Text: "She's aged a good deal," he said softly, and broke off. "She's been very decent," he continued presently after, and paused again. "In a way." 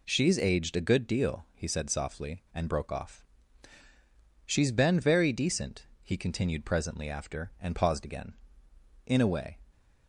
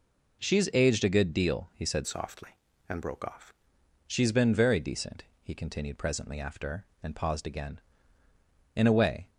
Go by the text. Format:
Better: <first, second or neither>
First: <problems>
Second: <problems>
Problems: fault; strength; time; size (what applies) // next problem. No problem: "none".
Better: first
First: none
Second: changes voice from "softly" to "off"; from 2.0 to 3.5 s; 1.5 s long